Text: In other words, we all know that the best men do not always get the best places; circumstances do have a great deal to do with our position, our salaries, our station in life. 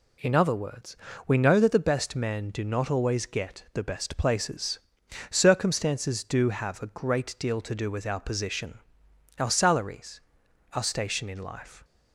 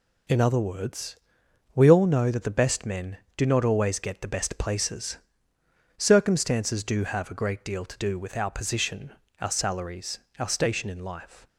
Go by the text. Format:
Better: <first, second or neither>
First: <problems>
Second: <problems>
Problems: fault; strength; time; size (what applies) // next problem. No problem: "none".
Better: second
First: skips "all"; at 1.3 s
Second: none